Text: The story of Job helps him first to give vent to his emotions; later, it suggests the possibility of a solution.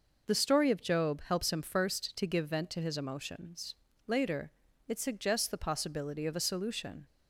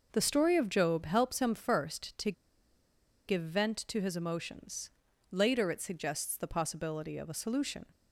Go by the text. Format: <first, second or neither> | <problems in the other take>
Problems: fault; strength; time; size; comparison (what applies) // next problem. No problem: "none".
first | pauses between "to" and "give"; noticeable; at 2.3 s; 0.95 s long